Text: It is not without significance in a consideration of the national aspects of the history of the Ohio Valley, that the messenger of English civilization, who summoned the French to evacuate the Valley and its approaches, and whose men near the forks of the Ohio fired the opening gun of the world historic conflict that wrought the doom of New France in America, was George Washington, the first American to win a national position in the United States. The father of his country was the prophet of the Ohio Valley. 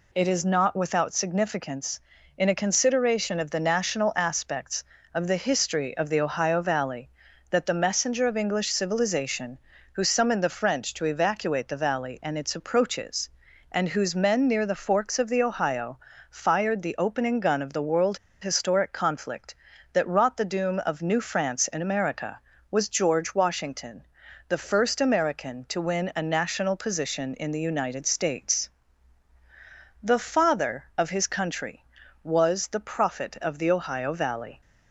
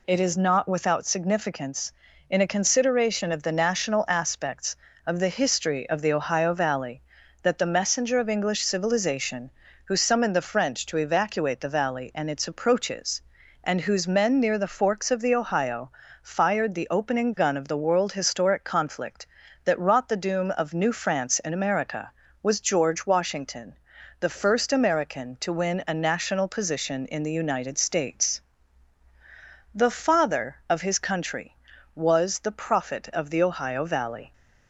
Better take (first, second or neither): second